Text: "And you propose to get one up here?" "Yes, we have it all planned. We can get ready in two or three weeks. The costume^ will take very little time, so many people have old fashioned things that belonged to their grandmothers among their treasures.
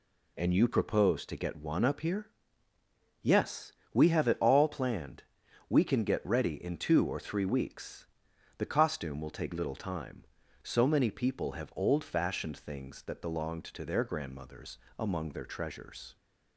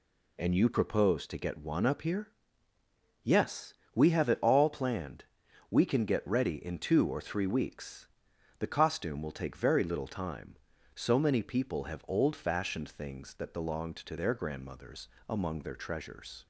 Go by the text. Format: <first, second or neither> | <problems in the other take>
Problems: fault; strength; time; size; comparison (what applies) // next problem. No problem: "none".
second | skips "very"; at 9.5 s // pauses between "grandmothers" and "among"; slight; at 14.7 s; 0.22 s long; slight in the second